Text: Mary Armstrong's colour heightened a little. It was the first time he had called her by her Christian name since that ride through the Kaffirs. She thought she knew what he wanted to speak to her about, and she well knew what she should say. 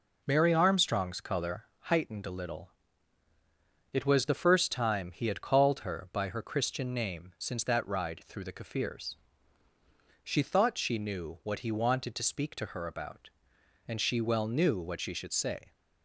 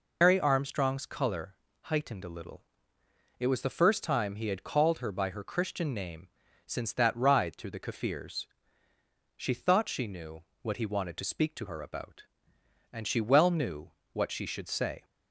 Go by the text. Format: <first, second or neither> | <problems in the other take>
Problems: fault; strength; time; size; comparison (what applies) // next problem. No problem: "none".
first | loses the start of "Mary"; at 0.2 s; 150 ms // pauses between "colour" and "heightened"; slight; at 1.5 s; 0.28 s long // pauses between "name" and "since"; at 6.2 s; 0.38 s long // pauses between "knew" and "what"; slight; at 10.4 s; 0.20 s long // pauses between "knew" and "what"; slight; at 13.9 s; 0.22 s long